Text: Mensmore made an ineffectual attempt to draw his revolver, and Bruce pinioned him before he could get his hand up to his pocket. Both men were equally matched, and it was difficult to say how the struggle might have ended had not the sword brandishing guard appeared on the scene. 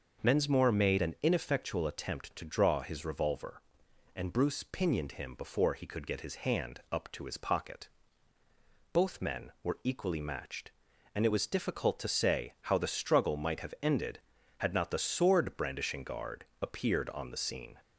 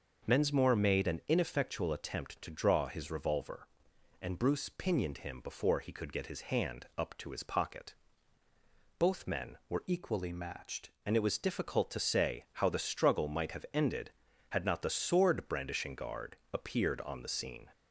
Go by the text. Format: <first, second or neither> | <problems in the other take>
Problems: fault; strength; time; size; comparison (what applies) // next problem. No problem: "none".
first | starts louder than the rest; noticeable; until 1.3 s; 6 dB; also in the first // changes voice from "equally" to "matched"; from 9.8 to 10.9 s; 1.1 s long // pauses between "guard" and "appeared"; slight; at 16.3 s; 0.18 s long; slight in the first